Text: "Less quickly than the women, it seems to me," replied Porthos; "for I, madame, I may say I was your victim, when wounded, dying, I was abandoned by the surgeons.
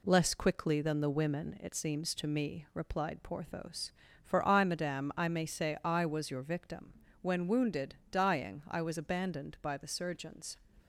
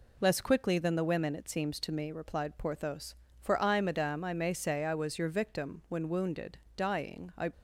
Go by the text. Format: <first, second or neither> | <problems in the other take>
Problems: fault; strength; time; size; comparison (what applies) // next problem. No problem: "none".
first | stops before "was abandoned by the surgeons"; at 7.5 s